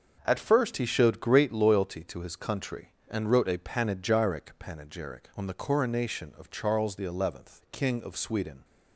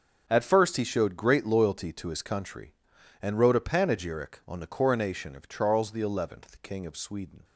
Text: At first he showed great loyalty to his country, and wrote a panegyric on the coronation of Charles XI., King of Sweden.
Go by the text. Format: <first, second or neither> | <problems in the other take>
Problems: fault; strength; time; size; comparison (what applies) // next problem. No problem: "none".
second | starts louder than the rest; until 1.2 s; 6.5 dB; also in the second // says "panegyric" twice; at 4.5 s